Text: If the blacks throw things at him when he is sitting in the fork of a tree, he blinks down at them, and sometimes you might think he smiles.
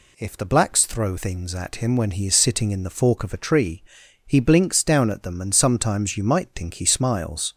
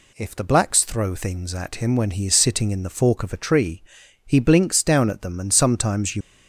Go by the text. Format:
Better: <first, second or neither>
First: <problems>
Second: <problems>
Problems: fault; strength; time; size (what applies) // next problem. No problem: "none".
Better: first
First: none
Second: stops before "might think he smiles"; at 6.2 s